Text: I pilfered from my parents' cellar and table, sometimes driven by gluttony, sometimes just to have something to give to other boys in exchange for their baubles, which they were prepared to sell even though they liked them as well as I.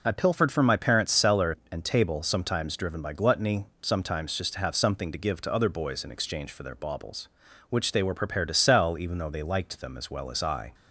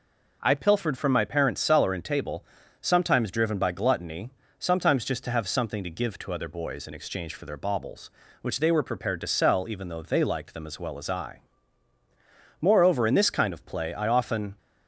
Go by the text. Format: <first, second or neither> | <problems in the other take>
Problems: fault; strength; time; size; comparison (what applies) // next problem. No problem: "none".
first | goes on to say "Moreover in this kind of play I often"; strong; from 12.5 s on; 1.9 s long